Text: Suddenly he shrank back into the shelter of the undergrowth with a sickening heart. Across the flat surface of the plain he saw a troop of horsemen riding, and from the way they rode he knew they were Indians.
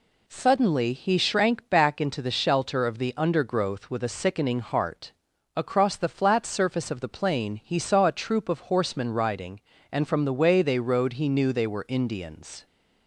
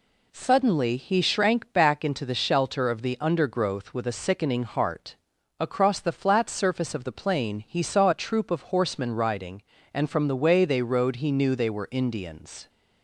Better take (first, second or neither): neither